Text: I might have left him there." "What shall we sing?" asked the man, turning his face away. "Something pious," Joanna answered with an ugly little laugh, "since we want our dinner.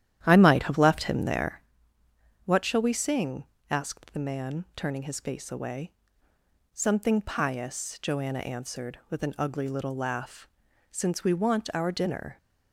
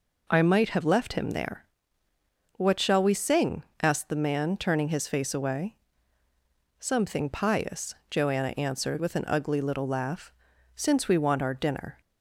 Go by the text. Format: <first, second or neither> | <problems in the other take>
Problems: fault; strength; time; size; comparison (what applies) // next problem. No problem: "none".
second | starts louder than the rest; strong; until 1.7 s; 11 dB